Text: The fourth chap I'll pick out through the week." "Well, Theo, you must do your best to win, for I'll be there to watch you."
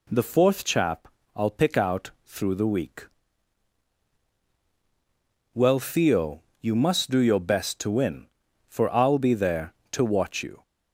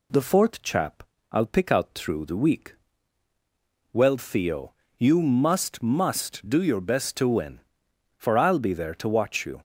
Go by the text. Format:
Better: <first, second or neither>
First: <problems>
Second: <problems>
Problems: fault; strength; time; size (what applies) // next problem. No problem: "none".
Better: first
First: pauses between "chap" and "I'll"; slight; at 1.0 s; 0.30 s long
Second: pauses between "chap" and "I'll"; slight; at 1.0 s; 0.26 s long // says "must" twice; at 5.8 s